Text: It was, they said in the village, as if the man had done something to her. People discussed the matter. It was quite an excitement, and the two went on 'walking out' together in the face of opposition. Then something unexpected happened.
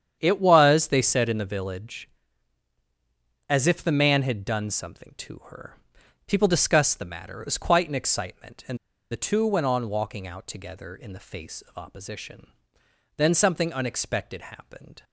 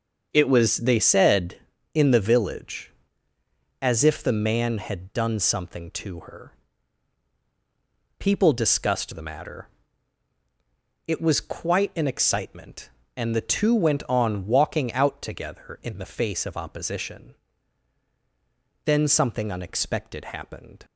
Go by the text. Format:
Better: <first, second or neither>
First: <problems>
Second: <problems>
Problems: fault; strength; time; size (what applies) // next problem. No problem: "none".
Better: second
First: starts louder than the rest; strong; until 1.2 s; 8.5 dB // pauses between "and" and "the"; slight; at 8.7 s; 0.34 s long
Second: starts louder than the rest; until 1.3 s; 7 dB